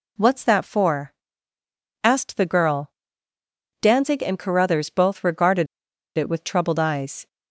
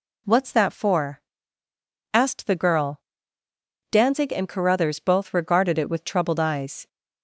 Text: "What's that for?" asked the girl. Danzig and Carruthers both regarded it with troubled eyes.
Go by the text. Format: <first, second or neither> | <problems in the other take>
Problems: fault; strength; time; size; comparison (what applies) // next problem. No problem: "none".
second | pauses between "regarded" and "it"; noticeable; at 5.6 s; 0.50 s long